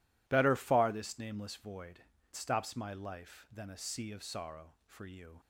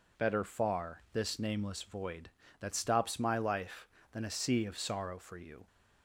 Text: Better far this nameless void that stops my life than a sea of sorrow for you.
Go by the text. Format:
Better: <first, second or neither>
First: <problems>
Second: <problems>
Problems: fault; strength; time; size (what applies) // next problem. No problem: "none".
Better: second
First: skips "that"; at 2.1 s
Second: none